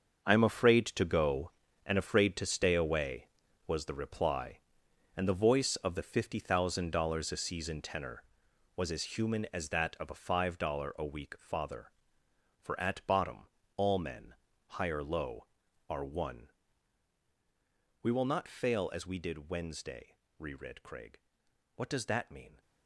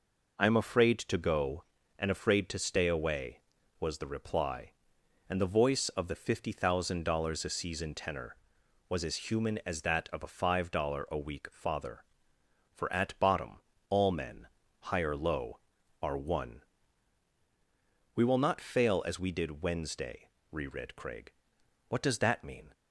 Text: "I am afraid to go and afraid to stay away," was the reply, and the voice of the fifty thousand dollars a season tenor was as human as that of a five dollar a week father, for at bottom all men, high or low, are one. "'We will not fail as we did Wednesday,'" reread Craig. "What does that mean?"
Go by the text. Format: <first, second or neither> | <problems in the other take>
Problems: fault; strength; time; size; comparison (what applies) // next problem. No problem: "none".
second | gets quieter; strong; throughout; 12 dB // pauses between "bottom" and "all"; slight; at 13.4 s; 0.26 s long; slight in the second